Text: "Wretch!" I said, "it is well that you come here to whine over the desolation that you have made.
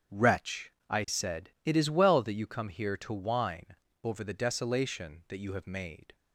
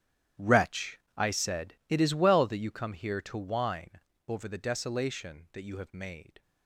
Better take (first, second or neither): first